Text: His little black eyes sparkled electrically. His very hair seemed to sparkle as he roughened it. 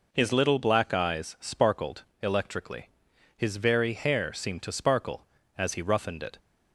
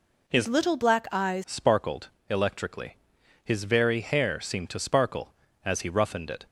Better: first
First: pauses between "sparkled" and "electrically"; slight; at 2.0 s; 0.20 s long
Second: changes voice from "little" to "eyes"; from 0.4 to 1.4 s; 1.0 s long // pauses between "sparkled" and "electrically"; slight; at 2.0 s; 0.22 s long

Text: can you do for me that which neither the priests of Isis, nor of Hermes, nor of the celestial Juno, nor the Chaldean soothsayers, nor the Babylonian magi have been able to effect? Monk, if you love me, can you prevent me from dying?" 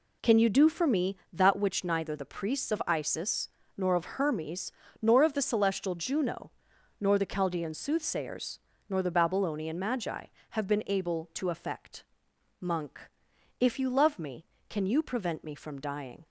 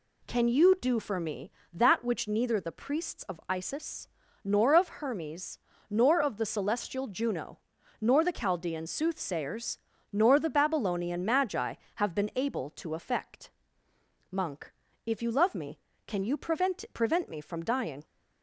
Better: first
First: none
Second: says "prevent" twice; at 16.9 s

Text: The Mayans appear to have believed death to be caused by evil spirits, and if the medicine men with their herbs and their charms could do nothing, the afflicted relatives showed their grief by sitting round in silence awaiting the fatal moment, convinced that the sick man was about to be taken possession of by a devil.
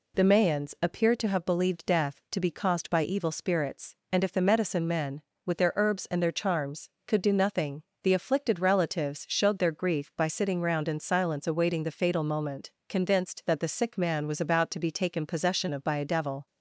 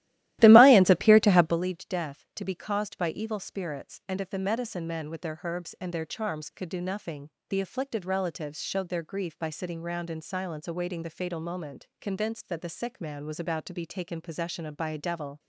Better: first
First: none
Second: starts louder than the rest; strong; until 1.6 s; 15 dB

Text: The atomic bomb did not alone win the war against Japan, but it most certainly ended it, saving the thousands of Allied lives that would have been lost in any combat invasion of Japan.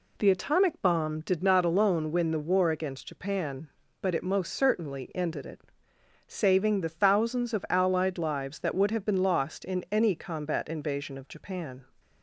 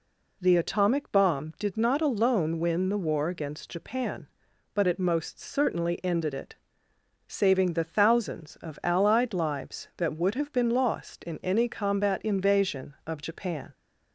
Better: neither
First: none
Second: none

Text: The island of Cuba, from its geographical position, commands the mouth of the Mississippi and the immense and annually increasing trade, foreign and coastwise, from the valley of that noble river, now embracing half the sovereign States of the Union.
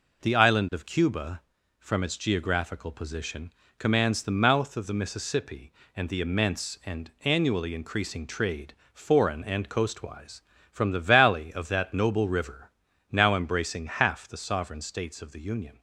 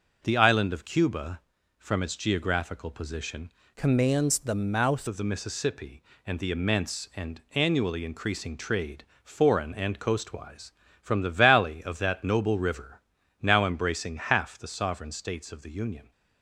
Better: first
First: none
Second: changes voice from "commands" to "mouth"; from 3.7 to 5.0 s; 1.3 s long

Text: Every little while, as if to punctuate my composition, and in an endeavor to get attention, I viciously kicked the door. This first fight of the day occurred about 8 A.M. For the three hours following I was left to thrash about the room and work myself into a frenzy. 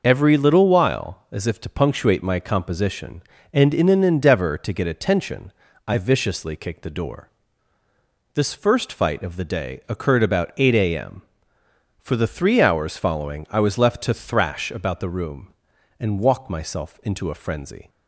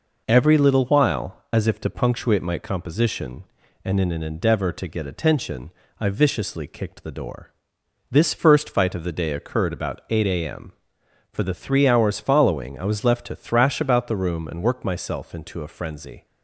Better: second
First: says "walk" for "work"; at 16.2 s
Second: none

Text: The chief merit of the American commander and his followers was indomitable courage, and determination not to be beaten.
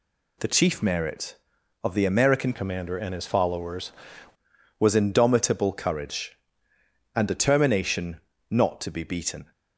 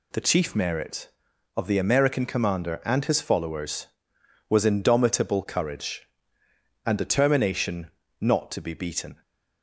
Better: second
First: changes voice from "commander" to "followers"; from 2.5 to 3.9 s; 1.4 s long // pauses between "determination" and "not"; slight; at 8.2 s; 0.28 s long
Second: pauses between "determination" and "not"; slight; at 7.9 s; 0.28 s long

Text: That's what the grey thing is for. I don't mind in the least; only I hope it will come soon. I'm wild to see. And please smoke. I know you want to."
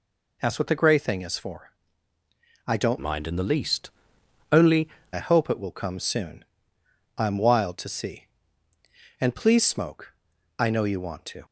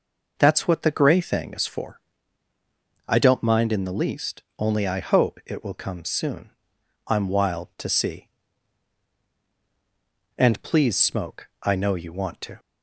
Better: second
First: changes voice from "mind" to "only"; from 3.0 to 4.8 s; 1.8 s long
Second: none

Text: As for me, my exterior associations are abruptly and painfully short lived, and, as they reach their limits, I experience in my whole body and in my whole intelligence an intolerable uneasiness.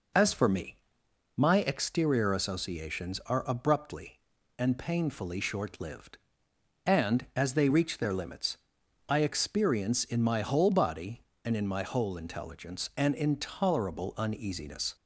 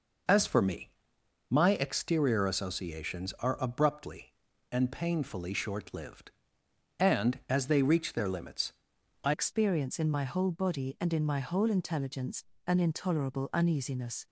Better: first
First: none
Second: changes voice at "experience"; from 9.3 s on; 4.9 s long // pauses between "intelligence" and "an"; slight; at 12.4 s; 0.22 s long

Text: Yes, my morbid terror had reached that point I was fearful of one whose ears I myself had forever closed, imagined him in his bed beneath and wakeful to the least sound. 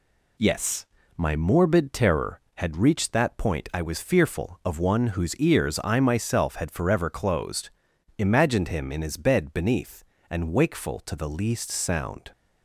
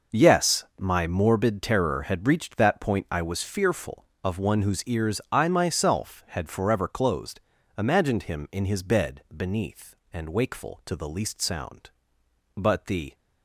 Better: first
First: none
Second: goes on to say "But the"; from 12.5 s on; 0.58 s long

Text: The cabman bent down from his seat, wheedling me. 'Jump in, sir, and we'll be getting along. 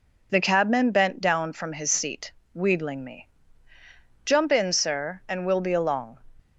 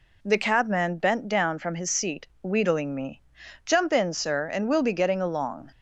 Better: second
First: skips "getting"; at 5.7 s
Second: none

